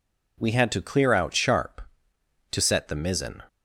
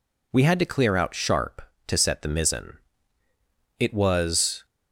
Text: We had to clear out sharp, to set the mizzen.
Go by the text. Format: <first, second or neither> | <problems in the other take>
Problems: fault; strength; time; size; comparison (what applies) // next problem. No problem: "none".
first | goes on to say "It was"; noticeable; from 3.7 s on; 0.86 s long